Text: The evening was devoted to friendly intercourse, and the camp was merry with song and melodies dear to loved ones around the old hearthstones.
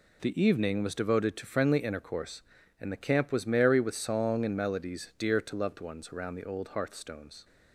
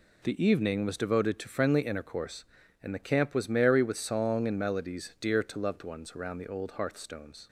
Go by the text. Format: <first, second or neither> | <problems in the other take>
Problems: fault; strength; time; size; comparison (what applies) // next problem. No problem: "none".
neither | none